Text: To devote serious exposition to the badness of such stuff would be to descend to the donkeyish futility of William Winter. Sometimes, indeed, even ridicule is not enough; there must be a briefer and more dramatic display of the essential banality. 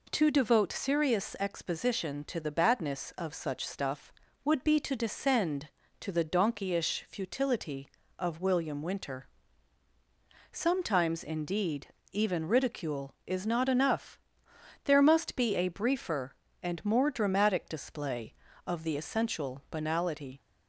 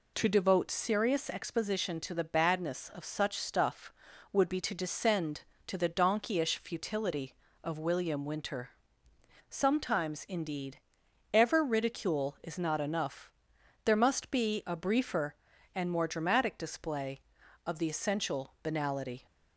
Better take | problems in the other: first | says "ever" for "even"; at 11.3 s

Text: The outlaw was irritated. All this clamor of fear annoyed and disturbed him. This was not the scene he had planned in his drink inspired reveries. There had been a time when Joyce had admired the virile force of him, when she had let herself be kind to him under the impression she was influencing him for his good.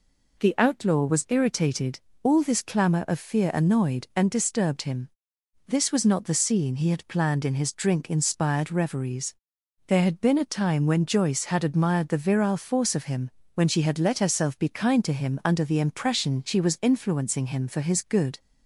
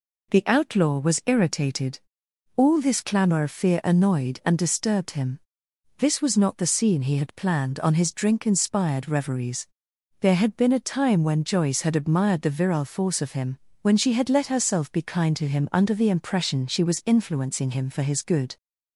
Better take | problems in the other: first | says "on" for "in"; at 7.7 s

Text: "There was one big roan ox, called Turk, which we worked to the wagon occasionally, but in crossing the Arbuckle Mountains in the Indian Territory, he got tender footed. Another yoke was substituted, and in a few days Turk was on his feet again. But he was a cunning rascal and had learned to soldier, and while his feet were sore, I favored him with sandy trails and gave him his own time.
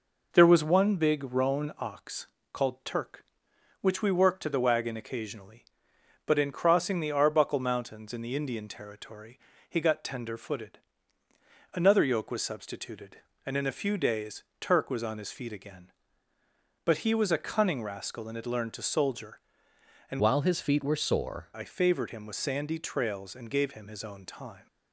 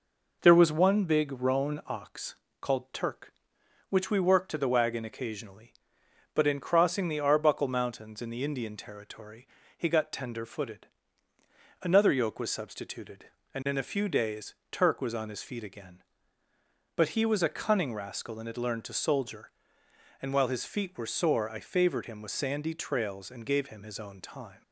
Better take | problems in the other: second | pauses between "days" and "Turk"; slight; at 14.4 s; 0.18 s long; slight in the second // changes voice from "while" to "sore"; from 20.1 to 21.4 s; 1.3 s long

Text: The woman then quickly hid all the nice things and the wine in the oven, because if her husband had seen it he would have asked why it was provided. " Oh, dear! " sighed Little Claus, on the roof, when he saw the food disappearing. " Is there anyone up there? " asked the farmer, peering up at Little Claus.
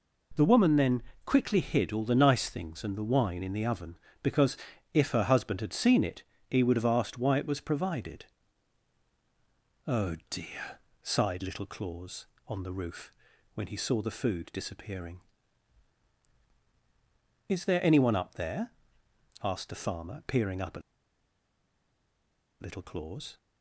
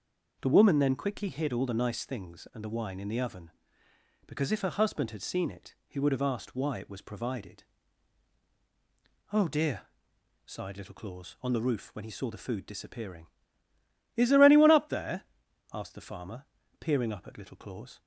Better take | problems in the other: second | pauses between "then" and "quickly"; slight; at 1.0 s; 0.22 s long // pauses between "because" and "if"; slight; at 4.5 s; 0.36 s long // pauses between "it" and "he"; slight; at 6.2 s; 0.26 s long // pauses between "at" and "Little"; strong; at 20.8 s; 1.8 s long

